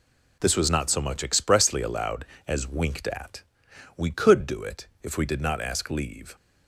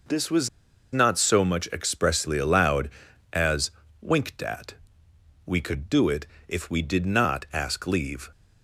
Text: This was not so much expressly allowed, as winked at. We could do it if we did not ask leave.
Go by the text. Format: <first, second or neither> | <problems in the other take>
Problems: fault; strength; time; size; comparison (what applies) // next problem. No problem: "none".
first | pauses between "was" and "not"; at 0.4 s; 0.43 s long // pauses between "as" and "winked"; slight; at 3.7 s; 0.30 s long // pauses between "it" and "if"; slight; at 6.2 s; 0.22 s long; slight in the first